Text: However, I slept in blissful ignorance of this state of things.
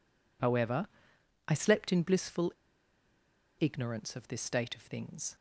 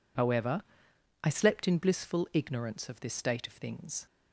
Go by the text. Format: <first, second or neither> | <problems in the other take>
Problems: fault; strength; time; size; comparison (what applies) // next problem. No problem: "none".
second | pauses between "blissful" and "ignorance"; at 2.5 s; 1.0 s long